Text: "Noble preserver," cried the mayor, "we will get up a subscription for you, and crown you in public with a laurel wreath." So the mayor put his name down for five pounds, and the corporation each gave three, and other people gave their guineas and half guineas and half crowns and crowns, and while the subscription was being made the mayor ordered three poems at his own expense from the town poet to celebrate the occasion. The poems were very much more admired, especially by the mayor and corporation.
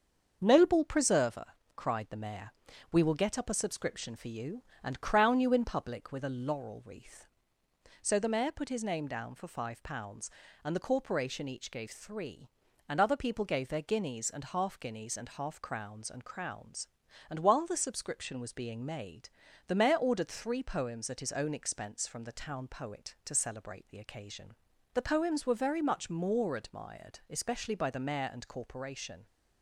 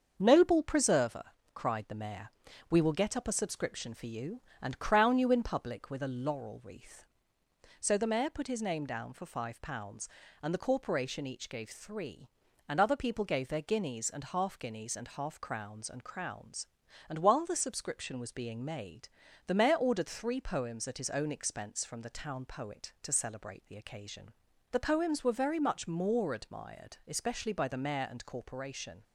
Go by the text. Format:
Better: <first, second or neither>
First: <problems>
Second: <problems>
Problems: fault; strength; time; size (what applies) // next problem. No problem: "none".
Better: neither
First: starts louder than the rest; until 1.4 s; 6.5 dB // pauses between "made" and "the"; slight; at 19.2 s; 0.36 s long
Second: starts louder than the rest; until 1.2 s; 6.5 dB // pauses between "made" and "the"; slight; at 19.0 s; 0.36 s long